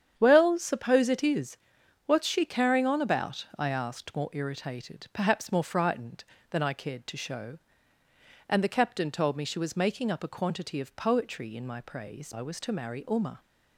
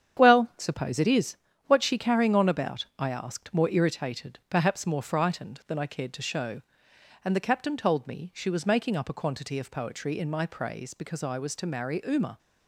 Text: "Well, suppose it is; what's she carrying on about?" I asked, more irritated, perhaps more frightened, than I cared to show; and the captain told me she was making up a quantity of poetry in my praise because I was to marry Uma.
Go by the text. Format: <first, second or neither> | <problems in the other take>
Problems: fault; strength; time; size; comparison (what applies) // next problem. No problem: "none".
second | starts louder than the rest; strong; until 1.1 s; 8.5 dB; strong in the second // skips "because"; at 12.3 s